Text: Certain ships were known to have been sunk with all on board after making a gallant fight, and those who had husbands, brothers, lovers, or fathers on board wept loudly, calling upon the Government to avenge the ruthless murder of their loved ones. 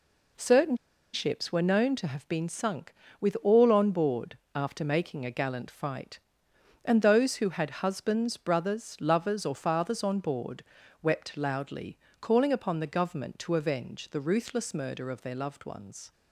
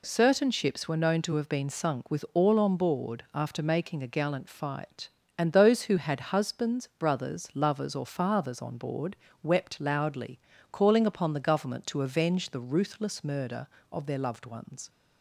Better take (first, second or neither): second